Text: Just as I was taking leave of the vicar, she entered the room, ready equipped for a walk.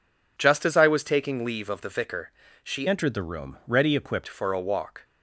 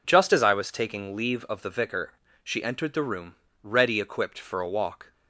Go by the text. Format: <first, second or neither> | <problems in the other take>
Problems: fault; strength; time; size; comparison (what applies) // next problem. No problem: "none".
second | changes voice from "entered" to "equipped"; from 2.8 to 4.2 s; 1.4 s long